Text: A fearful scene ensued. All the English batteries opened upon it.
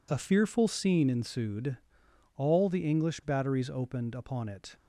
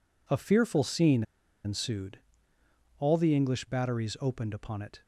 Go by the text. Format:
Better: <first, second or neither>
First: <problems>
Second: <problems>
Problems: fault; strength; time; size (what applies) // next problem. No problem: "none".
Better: first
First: none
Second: pauses between "scene" and "ensued"; at 1.2 s; 0.42 s long